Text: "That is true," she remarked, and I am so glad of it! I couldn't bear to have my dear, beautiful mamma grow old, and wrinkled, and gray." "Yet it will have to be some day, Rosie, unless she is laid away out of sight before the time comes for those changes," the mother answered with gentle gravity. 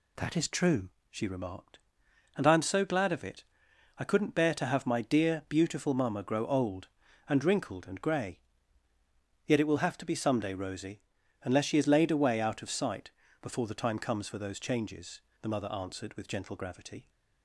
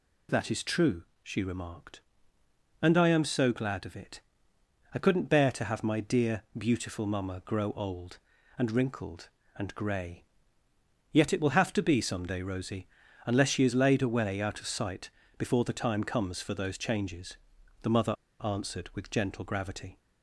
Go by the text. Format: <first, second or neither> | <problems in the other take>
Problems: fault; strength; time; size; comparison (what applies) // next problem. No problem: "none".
first | pauses between "sight" and "before"; slight; at 15.0 s; 0.26 s long; slight in the first // pauses between "mother" and "answered"; slight; at 18.1 s; 0.30 s long